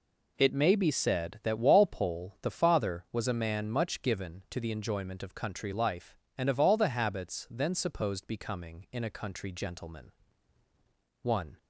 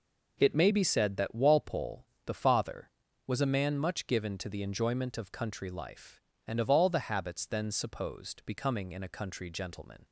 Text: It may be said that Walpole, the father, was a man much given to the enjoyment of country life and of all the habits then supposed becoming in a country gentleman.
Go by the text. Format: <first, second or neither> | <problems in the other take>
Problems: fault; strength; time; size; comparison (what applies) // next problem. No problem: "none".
second | goes on to say "One"; slight; from 11.2 s on; 0.36 s long